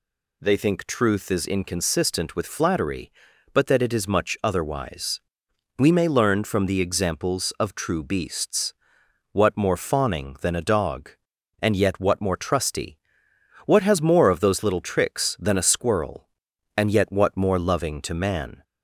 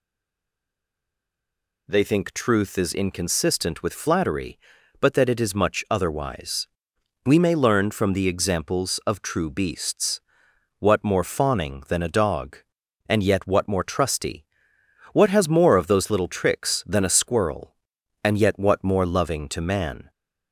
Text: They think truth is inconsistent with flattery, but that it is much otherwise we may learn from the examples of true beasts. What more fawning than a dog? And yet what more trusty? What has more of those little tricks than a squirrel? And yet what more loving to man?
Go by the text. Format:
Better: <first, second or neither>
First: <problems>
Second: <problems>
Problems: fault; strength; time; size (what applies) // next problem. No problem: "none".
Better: first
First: pauses between "otherwise" and "we"; noticeable; at 5.2 s; 0.58 s long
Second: stays silent before the first word; noticeable; until 1.8 s; 1.8 s long // pauses between "otherwise" and "we"; noticeable; at 6.6 s; 0.58 s long